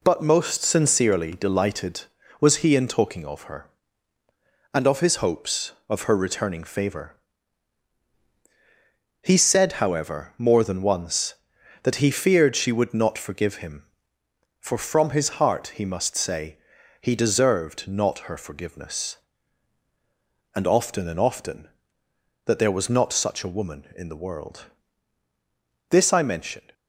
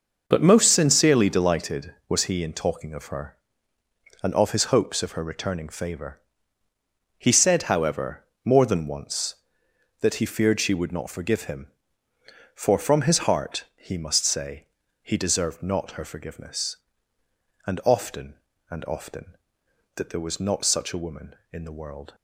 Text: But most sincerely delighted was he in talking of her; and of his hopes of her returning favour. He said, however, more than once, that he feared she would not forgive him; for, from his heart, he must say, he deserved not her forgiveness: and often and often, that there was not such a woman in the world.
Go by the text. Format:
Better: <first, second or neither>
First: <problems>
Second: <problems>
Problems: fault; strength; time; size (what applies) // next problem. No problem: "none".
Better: second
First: goes on to say "This I mention"; noticeable; from 25.9 s on; 0.82 s long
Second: none